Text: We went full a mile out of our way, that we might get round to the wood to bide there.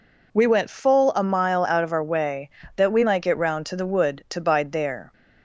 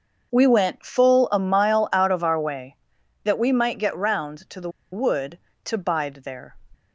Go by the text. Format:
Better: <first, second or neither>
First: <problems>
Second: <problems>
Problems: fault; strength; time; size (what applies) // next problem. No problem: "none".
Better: first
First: none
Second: starts louder than the rest; until 1.3 s; 6.5 dB // pauses between "the" and "wood"; slight; at 4.6 s; 0.22 s long